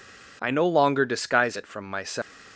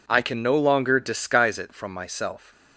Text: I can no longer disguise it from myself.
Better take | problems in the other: second | skips "can"; at 0.5 s

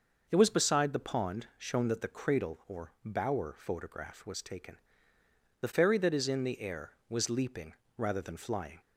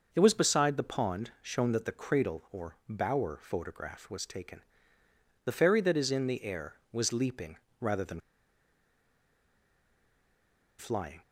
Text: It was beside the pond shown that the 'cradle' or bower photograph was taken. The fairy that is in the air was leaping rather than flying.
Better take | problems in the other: first | starts louder than the rest; noticeable; until 1.1 s; 6 dB // pauses between "leaping" and "rather"; slight; at 7.5 s; 0.22 s long; slight in the first // pauses between "than" and "flying"; strong; at 8.1 s; 2.5 s long

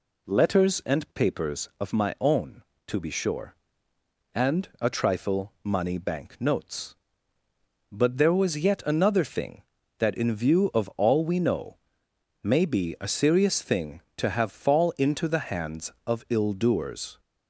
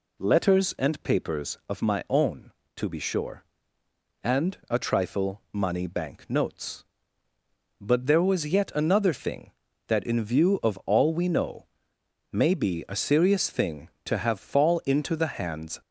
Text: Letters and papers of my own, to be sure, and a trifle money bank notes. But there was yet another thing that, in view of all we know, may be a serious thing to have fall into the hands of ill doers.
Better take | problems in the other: first | stops before "of ill doers"; at 15.8 s

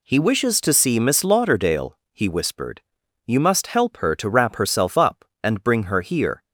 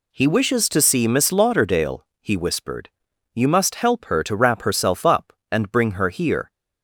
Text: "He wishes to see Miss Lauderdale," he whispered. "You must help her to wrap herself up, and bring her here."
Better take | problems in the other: neither | none

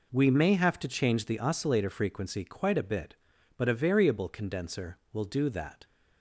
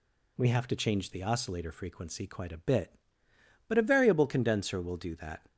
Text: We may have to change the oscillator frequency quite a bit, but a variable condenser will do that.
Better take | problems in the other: first | skips "may"; at 0.4 s

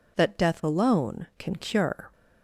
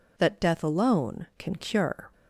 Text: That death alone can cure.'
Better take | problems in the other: neither | none

